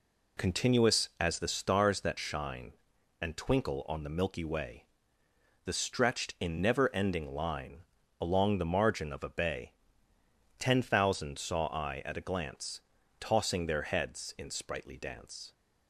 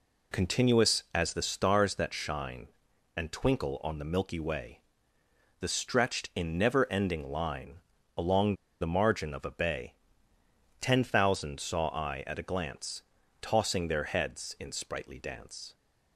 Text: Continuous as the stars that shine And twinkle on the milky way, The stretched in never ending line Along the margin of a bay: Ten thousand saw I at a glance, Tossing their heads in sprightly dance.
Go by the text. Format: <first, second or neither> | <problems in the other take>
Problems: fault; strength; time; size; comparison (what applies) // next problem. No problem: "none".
first | pauses between "line" and "Along"; slight; at 7.8 s; 0.36 s long; slight in the first // pauses between "Along" and "the"; slight; at 8.5 s; 0.26 s long